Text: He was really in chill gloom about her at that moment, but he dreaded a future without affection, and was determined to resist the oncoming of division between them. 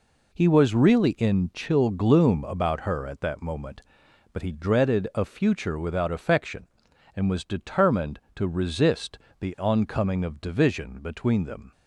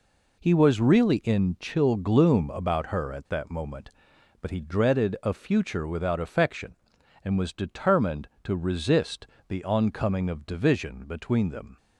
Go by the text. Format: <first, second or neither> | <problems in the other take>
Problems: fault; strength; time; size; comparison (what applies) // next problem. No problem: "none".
neither | pauses between "resist" and "the"; slight; the same in both